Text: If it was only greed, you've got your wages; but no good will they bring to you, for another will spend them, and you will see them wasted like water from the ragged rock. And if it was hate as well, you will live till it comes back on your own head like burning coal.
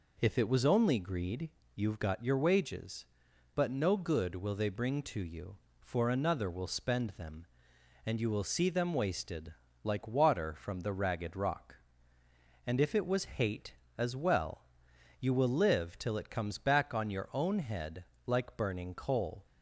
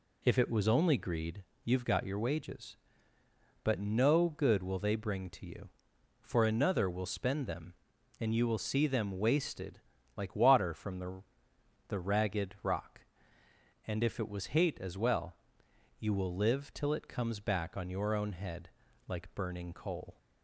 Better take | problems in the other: first | pauses between "wasted" and "like"; slight; at 9.8 s; 0.36 s long; slight in the first // says "the" twice; at 11.8 s // pauses between "head" and "like"; at 18.6 s; 0.38 s long; slight in the first

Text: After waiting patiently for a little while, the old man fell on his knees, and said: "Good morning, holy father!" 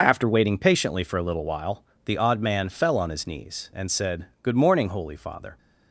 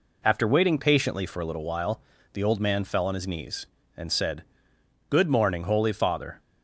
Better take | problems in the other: second | says "odd" for "old"; at 2.1 s

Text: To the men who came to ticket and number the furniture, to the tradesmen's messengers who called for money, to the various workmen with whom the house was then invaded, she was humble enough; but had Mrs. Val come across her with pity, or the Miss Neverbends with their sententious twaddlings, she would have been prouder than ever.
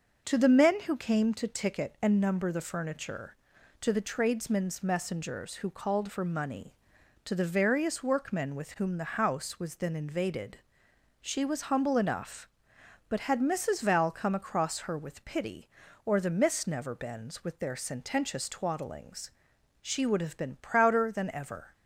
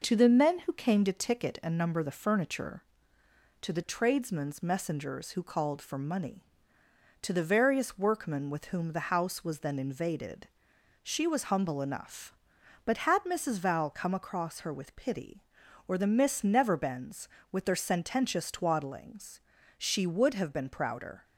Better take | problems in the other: first | stops before "than ever"; at 21.2 s

